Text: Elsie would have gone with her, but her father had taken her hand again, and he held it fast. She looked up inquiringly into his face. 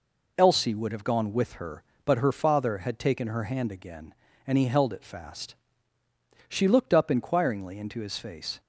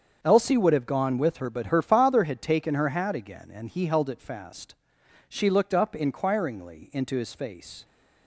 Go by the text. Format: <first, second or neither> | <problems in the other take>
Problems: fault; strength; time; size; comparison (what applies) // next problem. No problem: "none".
first | starts louder than the rest; until 1.2 s; 7 dB // says "hat" for "hand"; at 2.8 s